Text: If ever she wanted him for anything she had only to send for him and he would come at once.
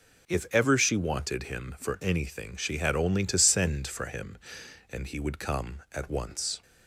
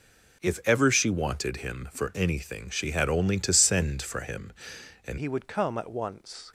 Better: first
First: none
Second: changes voice at "he"; from 5.1 s on; 1.4 s long

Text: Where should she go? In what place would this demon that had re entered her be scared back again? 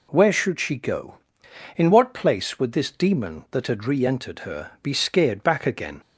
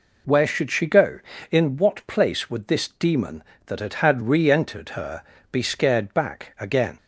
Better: first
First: none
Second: says "had" twice; at 3.9 s // pauses between "her" and "be"; slight; at 5.2 s; 0.30 s long

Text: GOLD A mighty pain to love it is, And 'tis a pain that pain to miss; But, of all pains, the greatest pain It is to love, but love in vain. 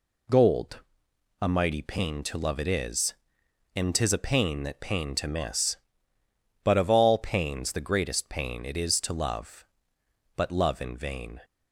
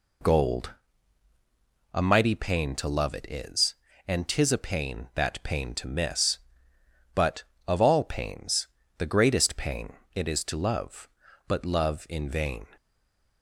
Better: first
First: pauses between "GOLD" and "A"; noticeable; at 0.8 s; 0.62 s long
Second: pauses between "GOLD" and "A"; at 0.7 s; 1.1 s long // pauses between "pain" and "It"; slight; at 9.9 s; 0.20 s long // stays silent after the last word; slight; from 12.7 s on; 0.7 s long

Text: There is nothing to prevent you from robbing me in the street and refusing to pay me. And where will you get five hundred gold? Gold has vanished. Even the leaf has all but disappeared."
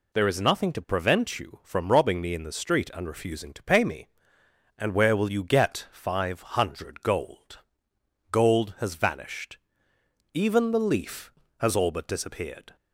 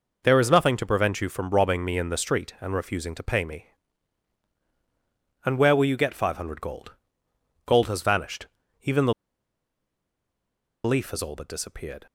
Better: first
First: none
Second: pauses between "the" and "leaf"; strong; at 9.1 s; 1.7 s long

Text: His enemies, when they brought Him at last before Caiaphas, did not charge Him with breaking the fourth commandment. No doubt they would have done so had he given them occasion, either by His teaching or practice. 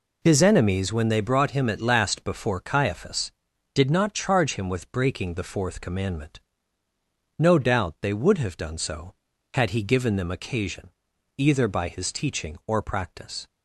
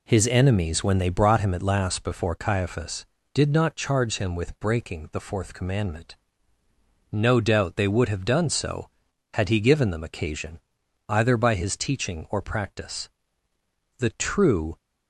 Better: first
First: none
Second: goes on to say "The true"; noticeable; from 13.9 s on; 0.78 s long

